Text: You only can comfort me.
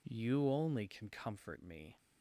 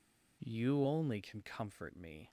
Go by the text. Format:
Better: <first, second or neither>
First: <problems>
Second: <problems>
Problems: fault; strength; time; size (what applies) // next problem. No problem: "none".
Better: neither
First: none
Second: none